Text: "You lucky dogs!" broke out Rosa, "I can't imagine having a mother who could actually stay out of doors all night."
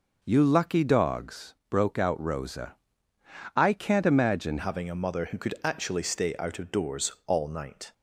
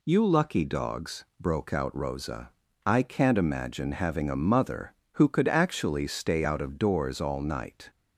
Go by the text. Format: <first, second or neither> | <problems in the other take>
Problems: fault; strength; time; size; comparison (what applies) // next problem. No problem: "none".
second | changes voice at "having"; from 4.5 s on; 3.4 s long